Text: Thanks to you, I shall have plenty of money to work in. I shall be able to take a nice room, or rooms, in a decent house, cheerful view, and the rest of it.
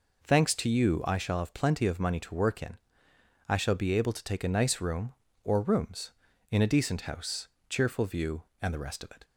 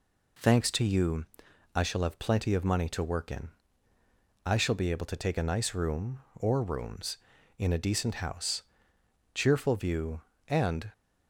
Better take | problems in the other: first | stops before "the rest of it"; at 10.9 s

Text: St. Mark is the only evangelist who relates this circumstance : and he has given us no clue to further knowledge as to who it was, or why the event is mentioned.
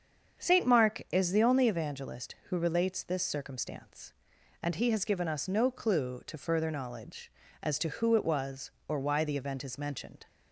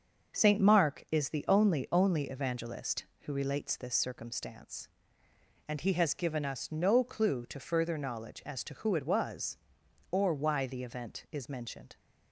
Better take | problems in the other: first | starts louder than the rest; until 1.4 s; 6.5 dB; strong in the first // says "only" twice; at 1.9 s

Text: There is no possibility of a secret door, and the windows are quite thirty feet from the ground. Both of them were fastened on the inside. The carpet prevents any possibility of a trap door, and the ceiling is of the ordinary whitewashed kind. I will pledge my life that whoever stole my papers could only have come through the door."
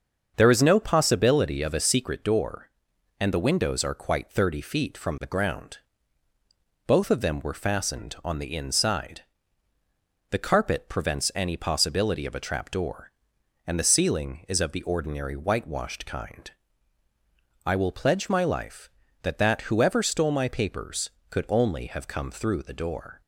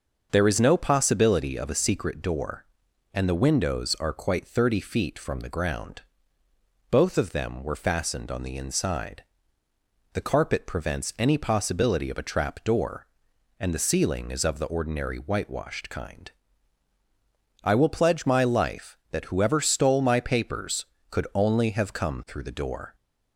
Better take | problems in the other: second | starts louder than the rest; until 1.3 s; 7 dB; also in the second // says "that" twice; at 19.3 s

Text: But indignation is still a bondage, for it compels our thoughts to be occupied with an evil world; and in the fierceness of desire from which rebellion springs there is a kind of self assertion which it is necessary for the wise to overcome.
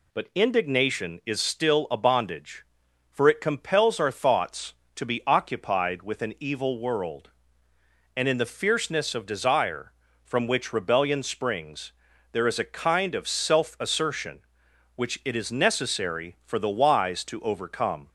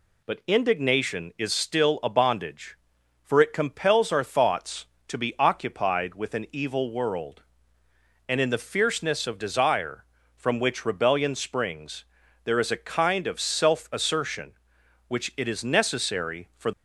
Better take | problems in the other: first | pauses between "springs" and "there"; at 12.0 s; 0.40 s long; also in the first // stops before "the wise to overcome"; at 16.7 s

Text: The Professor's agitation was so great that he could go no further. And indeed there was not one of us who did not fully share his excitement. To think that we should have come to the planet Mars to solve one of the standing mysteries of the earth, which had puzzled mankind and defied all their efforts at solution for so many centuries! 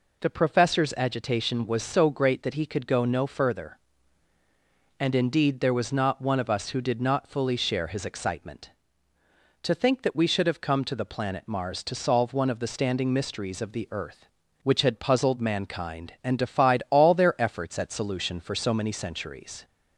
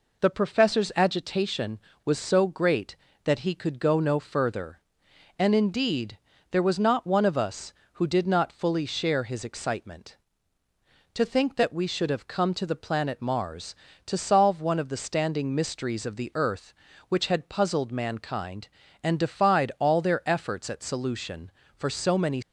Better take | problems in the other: first | pauses between "indeed" and "there"; slight; at 6.1 s; 0.32 s long // stops before "centuries"; at 22.4 s

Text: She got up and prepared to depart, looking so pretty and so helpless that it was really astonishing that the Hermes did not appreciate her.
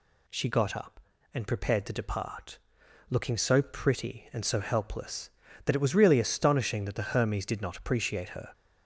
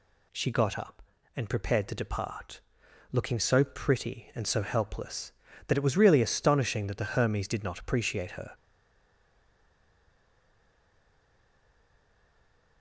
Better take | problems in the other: first | stays silent after the last word; strong; from 8.5 s on; 4.3 s long

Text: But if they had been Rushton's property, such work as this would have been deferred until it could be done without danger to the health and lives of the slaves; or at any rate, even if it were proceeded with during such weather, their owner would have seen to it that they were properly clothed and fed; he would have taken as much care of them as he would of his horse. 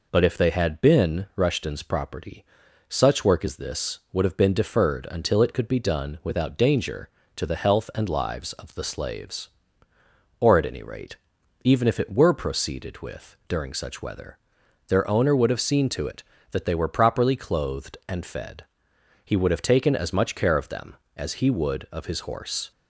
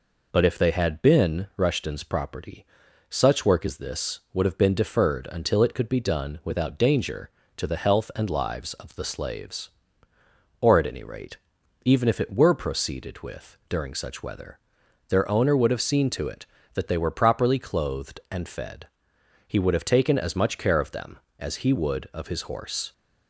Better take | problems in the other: neither | none

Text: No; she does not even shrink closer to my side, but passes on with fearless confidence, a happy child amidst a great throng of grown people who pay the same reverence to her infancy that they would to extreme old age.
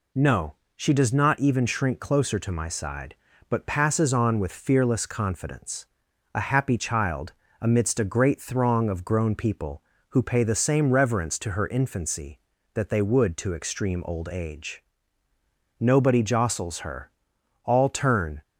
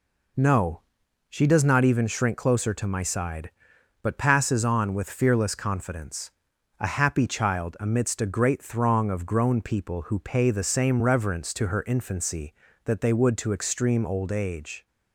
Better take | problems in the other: second | pauses between "child" and "amidst"; slight; at 7.3 s; 0.28 s long // goes on to say "Nobody jostles her all turn"; strong; from 15.8 s on; 2.6 s long

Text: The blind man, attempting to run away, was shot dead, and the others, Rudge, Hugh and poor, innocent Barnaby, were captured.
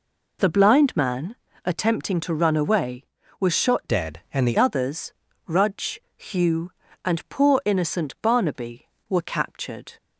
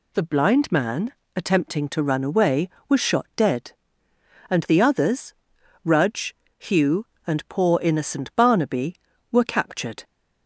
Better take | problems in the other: second | changes voice from "dead" to "the"; from 3.8 to 4.5 s; 0.7 s long

